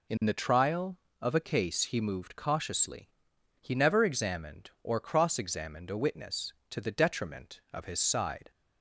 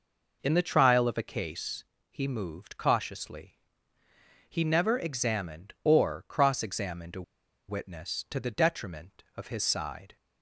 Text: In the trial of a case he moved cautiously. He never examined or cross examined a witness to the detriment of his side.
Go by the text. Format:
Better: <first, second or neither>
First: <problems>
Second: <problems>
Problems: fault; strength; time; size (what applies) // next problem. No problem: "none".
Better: first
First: none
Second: pauses between "case" and "he"; slight; at 1.8 s; 0.26 s long // pauses between "a" and "witness"; noticeable; at 7.2 s; 0.46 s long